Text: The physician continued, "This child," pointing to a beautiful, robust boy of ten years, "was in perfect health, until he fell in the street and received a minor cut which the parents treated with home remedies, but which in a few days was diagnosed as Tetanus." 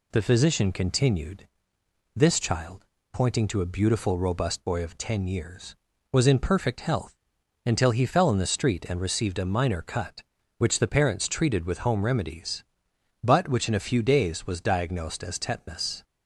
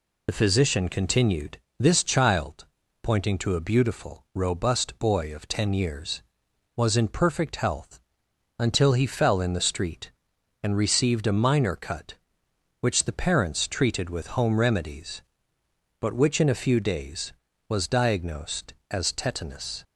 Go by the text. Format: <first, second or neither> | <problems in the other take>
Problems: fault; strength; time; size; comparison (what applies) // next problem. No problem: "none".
first | loses the start of "The"; at 0.2 s; 55 ms